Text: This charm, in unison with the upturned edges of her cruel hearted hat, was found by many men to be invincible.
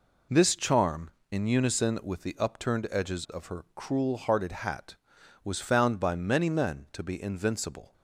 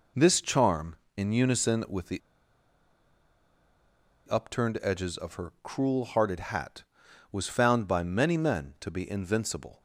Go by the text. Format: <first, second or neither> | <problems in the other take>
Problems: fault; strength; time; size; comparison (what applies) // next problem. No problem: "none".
first | pauses between "the" and "upturned"; strong; at 2.2 s; 2.0 s long